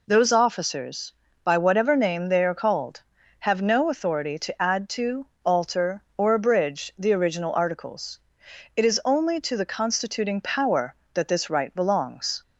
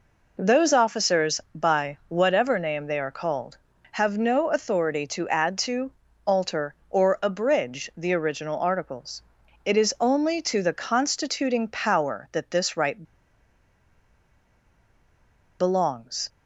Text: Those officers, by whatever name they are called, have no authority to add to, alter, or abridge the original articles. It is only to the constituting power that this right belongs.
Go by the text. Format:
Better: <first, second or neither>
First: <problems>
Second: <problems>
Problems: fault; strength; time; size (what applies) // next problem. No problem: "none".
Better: first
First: none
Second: pauses between "right" and "belongs"; strong; at 13.0 s; 2.5 s long